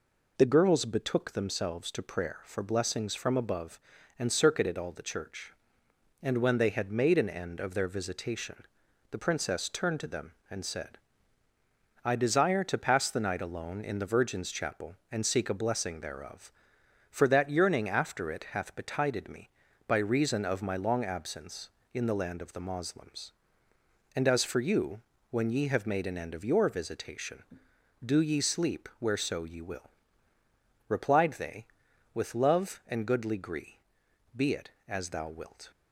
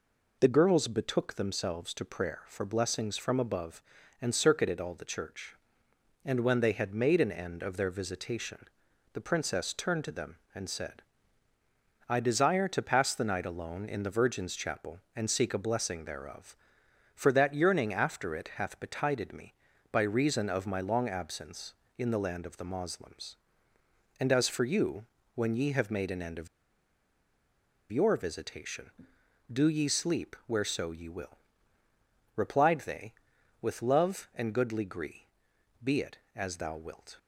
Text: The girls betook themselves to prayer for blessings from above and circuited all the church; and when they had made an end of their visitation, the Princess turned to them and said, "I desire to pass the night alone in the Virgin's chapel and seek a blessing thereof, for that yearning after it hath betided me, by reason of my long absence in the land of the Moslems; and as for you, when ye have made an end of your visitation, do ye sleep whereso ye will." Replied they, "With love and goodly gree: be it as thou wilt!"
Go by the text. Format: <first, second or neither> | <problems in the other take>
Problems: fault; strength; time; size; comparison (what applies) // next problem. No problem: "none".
first | pauses between "of" and "your"; strong; at 26.4 s; 1.4 s long